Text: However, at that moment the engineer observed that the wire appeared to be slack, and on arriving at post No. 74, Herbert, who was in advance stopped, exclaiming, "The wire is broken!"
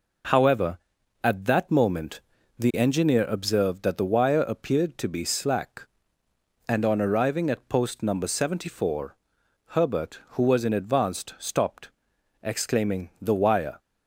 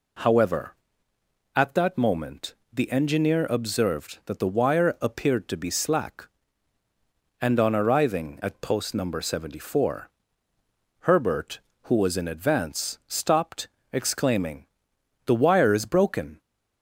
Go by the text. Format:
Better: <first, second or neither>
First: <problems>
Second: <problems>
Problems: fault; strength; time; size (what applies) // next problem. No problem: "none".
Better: second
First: pauses between "moment" and "the"; at 2.1 s; 0.38 s long // stops before "is broken"; at 13.7 s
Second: pauses between "moment" and "the"; slight; at 2.5 s; 0.18 s long